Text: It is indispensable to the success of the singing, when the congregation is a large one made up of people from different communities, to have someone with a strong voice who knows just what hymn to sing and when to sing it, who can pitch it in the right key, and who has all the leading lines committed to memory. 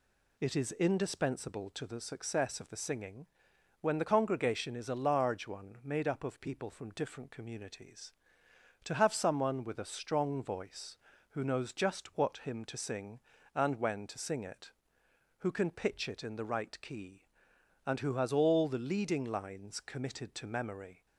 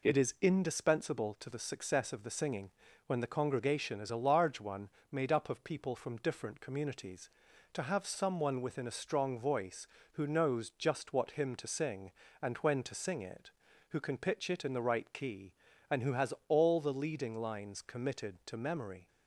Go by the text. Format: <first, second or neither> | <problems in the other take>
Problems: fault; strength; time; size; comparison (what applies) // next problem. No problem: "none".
first | pauses between "one" and "made"; slight; at 4.8 s; 0.24 s long // says "within" for "with"; at 8.6 s // pauses between "has" and "all"; slight; at 16.3 s; 0.16 s long